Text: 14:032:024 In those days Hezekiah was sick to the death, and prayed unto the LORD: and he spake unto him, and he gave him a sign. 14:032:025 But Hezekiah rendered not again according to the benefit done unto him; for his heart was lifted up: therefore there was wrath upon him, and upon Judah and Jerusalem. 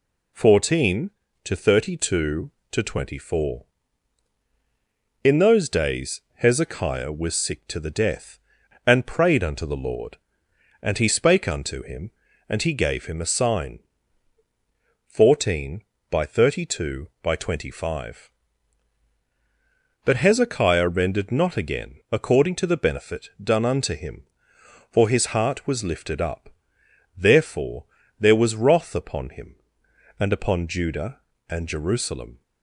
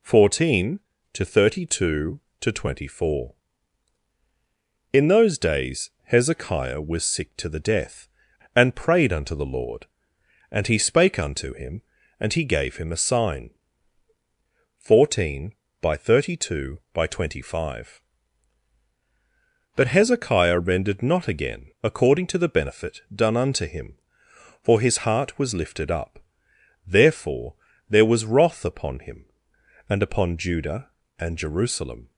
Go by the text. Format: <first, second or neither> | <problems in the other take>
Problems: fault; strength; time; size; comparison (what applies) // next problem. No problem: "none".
neither | pauses between "benefit" and "done"; slight; the same in both // pauses between "therefore" and "there"; slight; the same in both